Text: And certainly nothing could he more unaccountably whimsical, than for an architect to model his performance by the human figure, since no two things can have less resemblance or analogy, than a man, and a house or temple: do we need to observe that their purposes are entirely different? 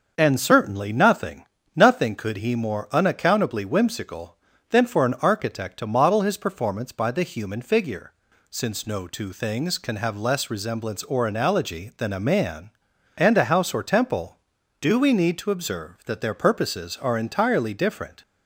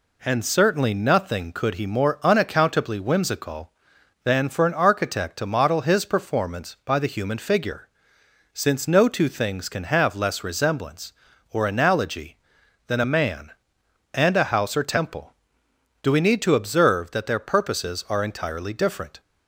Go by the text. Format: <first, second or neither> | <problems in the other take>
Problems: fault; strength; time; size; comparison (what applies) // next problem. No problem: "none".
second | starts louder than the rest; until 1.1 s; 6.5 dB // says "nothing" twice; at 1.7 s